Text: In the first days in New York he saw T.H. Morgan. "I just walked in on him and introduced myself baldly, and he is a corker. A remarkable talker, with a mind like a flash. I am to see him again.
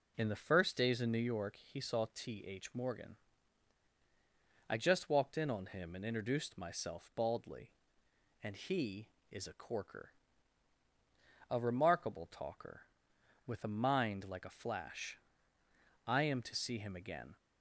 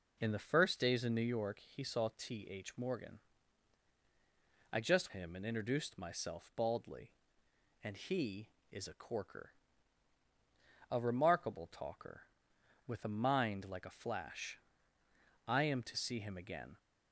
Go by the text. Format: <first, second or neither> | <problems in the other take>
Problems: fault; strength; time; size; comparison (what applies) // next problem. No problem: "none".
first | skips "walked in on"; at 5.1 s